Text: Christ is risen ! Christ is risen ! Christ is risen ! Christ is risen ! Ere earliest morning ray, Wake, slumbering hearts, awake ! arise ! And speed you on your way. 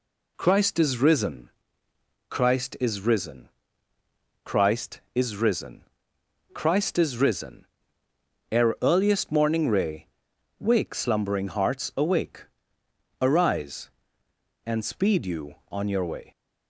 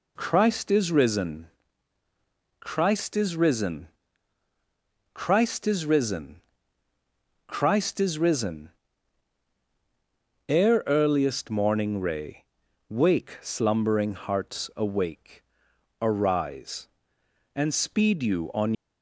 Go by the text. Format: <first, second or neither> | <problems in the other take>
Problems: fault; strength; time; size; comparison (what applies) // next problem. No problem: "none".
first | stops before "your way"; at 18.7 s